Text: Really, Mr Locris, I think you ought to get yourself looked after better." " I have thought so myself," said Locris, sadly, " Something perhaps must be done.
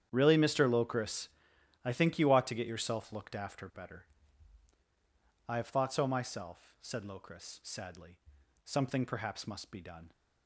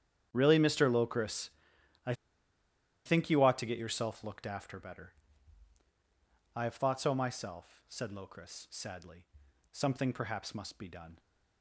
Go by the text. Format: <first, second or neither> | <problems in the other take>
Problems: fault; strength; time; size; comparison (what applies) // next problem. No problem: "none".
first | starts louder than the rest; strong; until 1.3 s; 9.5 dB; strong in the first // pauses between "I" and "think"; noticeable; at 2.1 s; 0.92 s long